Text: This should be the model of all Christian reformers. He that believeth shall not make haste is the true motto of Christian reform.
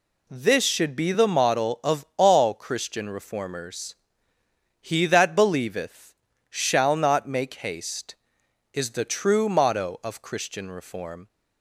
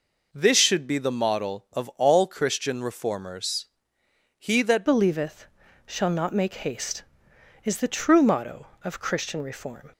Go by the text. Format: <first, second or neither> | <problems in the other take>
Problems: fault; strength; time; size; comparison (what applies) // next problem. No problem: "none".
first | changes voice at "believeth"; from 4.8 s on; 5.1 s long // pauses between "believeth" and "shall"; at 5.4 s; 0.40 s long; slight in the first